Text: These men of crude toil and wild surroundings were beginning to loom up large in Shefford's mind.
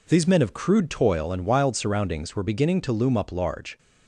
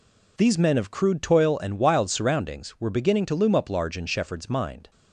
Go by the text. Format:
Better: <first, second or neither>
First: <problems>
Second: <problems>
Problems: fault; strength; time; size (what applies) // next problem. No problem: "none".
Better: second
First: stops before "in Shefford's mind"; at 3.7 s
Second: none